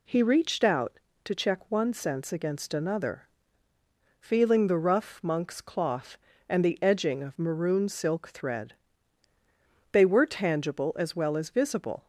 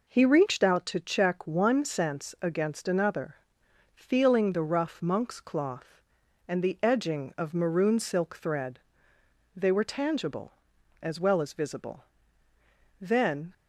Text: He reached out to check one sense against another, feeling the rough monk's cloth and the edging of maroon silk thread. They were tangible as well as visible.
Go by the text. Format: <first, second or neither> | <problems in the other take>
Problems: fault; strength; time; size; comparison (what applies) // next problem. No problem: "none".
first | goes on to say "Then"; from 13.0 s on; 0.52 s long